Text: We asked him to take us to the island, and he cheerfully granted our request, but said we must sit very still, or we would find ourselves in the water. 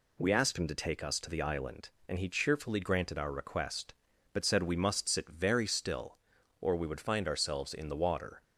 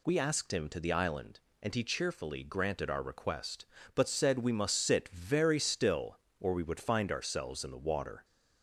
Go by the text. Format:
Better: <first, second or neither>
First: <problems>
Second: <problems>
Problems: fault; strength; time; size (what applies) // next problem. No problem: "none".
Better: first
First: none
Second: skips "to take us"; at 0.7 s